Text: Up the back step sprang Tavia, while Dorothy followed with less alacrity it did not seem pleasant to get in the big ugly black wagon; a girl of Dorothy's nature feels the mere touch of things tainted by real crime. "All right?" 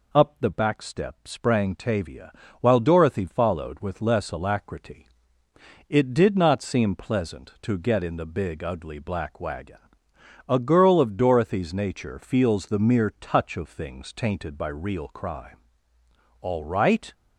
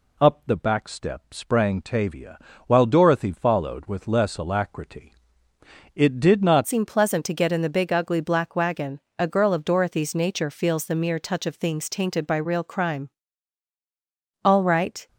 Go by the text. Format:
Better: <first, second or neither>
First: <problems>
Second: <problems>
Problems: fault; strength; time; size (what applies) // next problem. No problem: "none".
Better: first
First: pauses between "alacrity" and "it"; noticeable; at 5.0 s; 0.82 s long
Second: pauses between "alacrity" and "it"; noticeable; at 5.1 s; 0.82 s long // changes voice at "seem"; from 6.6 s on; 8.4 s long